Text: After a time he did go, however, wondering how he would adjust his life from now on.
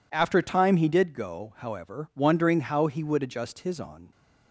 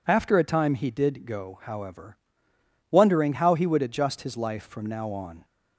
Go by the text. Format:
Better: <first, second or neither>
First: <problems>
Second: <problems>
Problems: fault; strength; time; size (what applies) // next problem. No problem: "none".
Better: second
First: skips "life from now"; at 3.7 s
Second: none